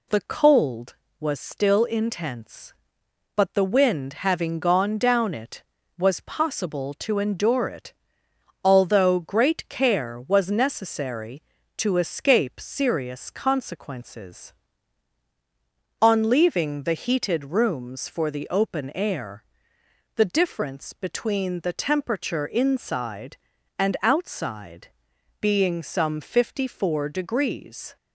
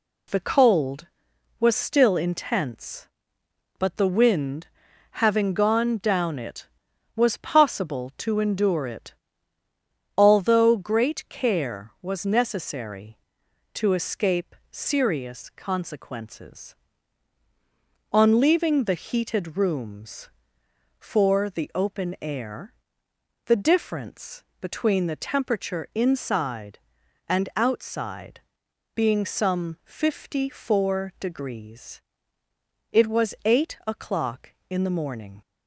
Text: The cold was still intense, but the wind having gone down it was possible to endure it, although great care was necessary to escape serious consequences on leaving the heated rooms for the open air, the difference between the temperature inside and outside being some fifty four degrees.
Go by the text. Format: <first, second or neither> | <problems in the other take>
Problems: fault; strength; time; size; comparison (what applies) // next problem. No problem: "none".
first | pauses between "wind" and "having"; at 4.6 s; 0.44 s long // pauses between "difference" and "between"; slight; at 24.4 s; 0.18 s long // pauses between "outside" and "being"; noticeable; at 28.4 s; 0.54 s long; noticeable in the first // goes on to say "It was eight o'clock in the morning"; strong; from 32.9 s on; 2.5 s long